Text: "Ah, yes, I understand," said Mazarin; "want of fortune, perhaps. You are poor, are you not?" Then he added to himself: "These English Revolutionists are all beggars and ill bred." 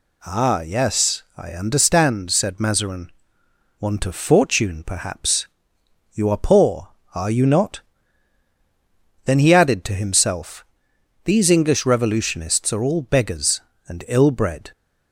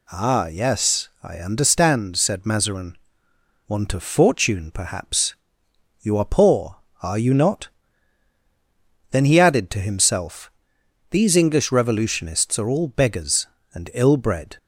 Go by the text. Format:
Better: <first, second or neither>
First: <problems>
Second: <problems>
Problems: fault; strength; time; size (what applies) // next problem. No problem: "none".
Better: neither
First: none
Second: none